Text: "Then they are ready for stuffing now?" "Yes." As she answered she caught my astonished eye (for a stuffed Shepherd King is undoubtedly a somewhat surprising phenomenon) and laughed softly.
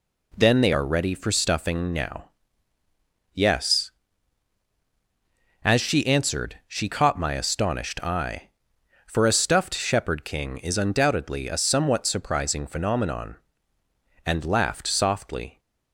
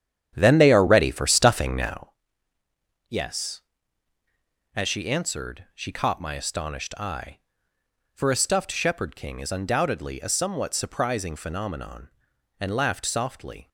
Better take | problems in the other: first | starts louder than the rest; strong; until 2.1 s; 9.5 dB

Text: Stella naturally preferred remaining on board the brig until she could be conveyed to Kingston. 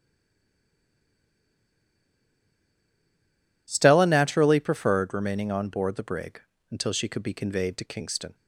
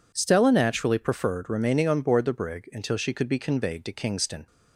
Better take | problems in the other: second | stays silent before the first word; strong; until 3.6 s; 3.6 s long // pauses between "brig" and "until"; slight; at 6.4 s; 0.30 s long

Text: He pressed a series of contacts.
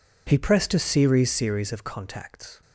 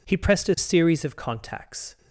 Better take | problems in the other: second | says "series" twice; at 1.3 s

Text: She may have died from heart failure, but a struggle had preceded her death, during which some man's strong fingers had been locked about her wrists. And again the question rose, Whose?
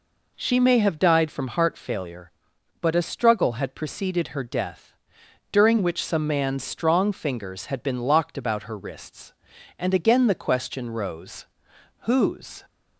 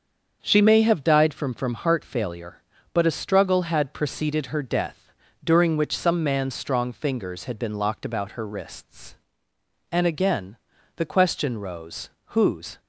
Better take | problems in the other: first | starts louder than the rest; until 1.4 s; 7 dB // says "from" twice; at 1.5 s // pauses between "again" and "the"; at 10.5 s; 0.40 s long

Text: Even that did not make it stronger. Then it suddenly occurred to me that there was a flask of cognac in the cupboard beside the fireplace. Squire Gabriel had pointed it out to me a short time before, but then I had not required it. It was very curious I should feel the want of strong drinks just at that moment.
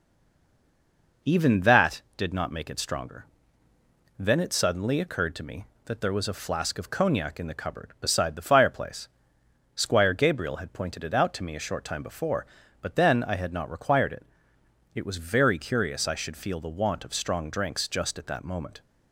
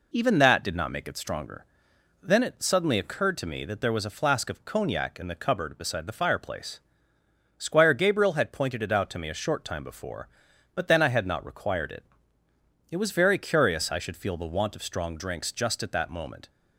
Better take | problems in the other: second | stays silent before the first word; noticeable; until 1.2 s; 1.2 s long

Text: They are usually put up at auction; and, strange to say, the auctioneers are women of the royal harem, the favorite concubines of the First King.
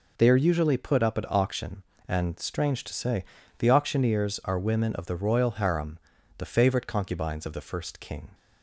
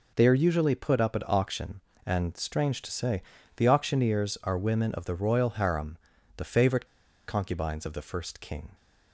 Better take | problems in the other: first | pauses between "favorite" and "concubines"; at 6.8 s; 0.42 s long

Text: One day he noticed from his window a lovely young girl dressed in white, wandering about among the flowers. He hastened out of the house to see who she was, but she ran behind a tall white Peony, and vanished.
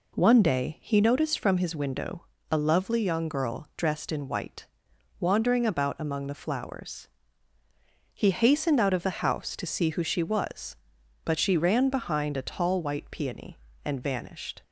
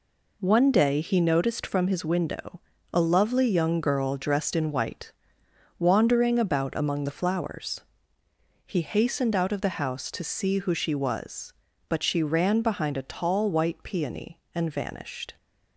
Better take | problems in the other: neither | pauses between "window" and "a"; slight; the same in both

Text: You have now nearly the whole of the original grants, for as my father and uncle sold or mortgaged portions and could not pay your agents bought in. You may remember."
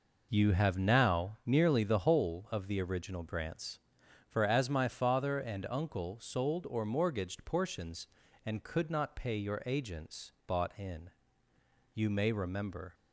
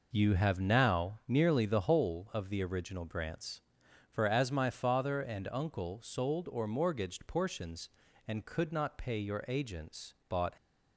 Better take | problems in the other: first | pauses between "agents" and "bought"; slight; at 10.1 s; 0.16 s long; slight in the first // stops before "in You may remember"; at 10.5 s

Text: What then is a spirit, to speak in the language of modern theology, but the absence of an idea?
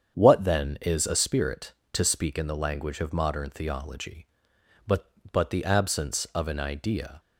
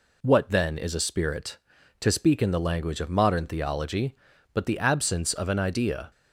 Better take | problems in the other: second | starts louder than the rest; strong; until 1.1 s; 7.5 dB // says "but" twice; at 5.2 s

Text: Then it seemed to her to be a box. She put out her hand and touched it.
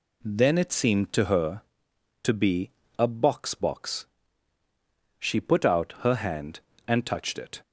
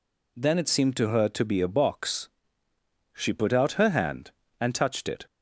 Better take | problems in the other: second | pauses between "be" and "a"; slight; at 2.6 s; 0.28 s long // says "box" twice; at 3.5 s

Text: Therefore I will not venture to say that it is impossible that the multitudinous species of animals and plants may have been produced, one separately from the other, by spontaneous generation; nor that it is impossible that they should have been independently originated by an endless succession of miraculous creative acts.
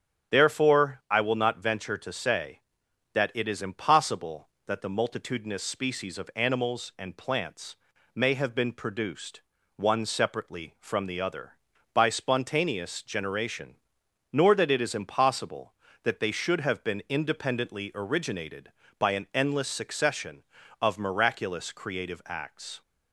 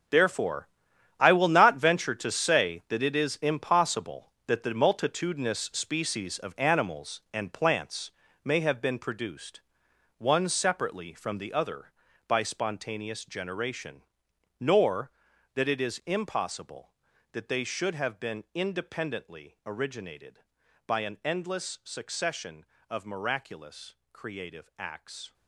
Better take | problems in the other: first | gets quieter; strong; throughout; 12 dB // starts louder than the rest; until 1.6 s; 6.5 dB; strong in the first // pauses between "Therefore" and "I"; noticeable; at 0.6 s; 0.52 s long // pauses between "plants" and "may"; slight; at 8.1 s; 0.34 s long; also in the first // pauses between "miraculous" and "creative"; slight; at 23.9 s; 0.18 s long

